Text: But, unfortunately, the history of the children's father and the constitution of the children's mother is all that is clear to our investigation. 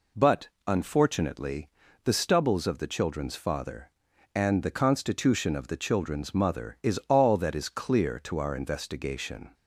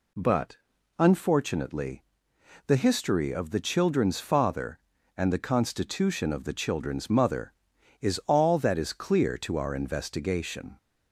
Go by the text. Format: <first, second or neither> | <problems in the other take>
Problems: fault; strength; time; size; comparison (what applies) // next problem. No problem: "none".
second | says "stubbles" for "history"; at 2.1 s